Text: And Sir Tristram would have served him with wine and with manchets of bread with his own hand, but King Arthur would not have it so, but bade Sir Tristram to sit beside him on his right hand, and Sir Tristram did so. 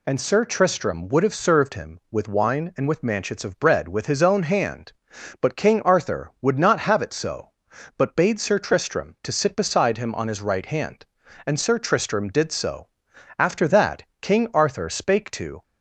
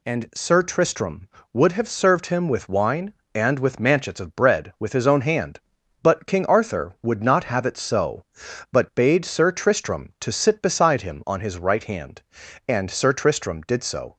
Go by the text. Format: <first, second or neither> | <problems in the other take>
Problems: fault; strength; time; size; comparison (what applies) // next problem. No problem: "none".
second | goes on to say "After that King Arthur spake to"; strong; from 13.3 s on; 2.2 s long